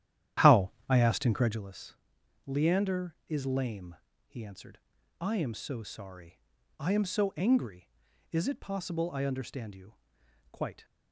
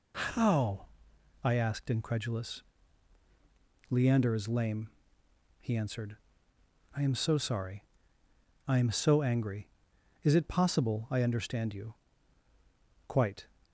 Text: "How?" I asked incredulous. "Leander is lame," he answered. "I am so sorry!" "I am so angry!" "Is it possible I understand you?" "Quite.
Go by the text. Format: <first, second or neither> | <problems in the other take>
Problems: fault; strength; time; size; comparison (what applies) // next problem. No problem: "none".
second | starts louder than the rest; strong; until 1.7 s; 11.5 dB